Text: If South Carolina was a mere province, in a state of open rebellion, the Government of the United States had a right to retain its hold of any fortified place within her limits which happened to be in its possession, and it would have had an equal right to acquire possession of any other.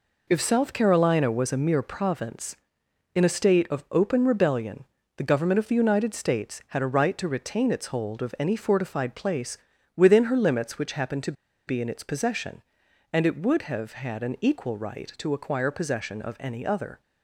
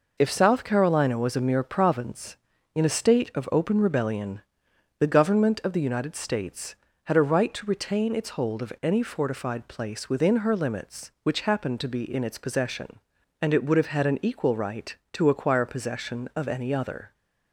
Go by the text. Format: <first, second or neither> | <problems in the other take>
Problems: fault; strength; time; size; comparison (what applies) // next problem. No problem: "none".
second | pauses between "place" and "within"; at 9.5 s; 0.40 s long // pauses between "to" and "be"; slight; at 11.3 s; 0.34 s long